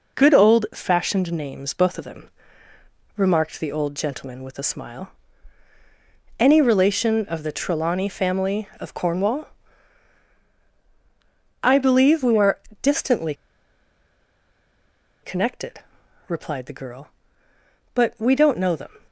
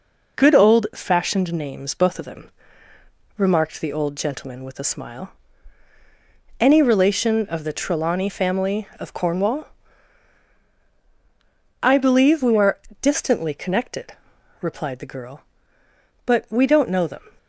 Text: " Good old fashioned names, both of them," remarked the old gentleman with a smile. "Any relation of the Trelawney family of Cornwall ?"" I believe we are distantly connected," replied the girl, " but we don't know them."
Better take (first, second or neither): second